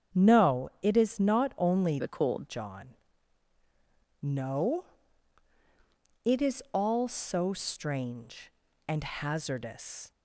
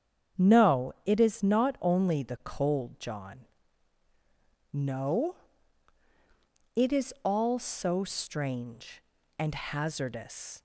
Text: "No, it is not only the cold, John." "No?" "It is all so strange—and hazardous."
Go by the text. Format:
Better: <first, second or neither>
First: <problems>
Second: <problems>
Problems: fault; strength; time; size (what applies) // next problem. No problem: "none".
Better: second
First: starts louder than the rest; strong; until 1.2 s; 8 dB // changes voice from "the" to "cold"; from 1.9 to 2.4 s; 0.5 s long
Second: starts louder than the rest; strong; until 1.5 s; 8 dB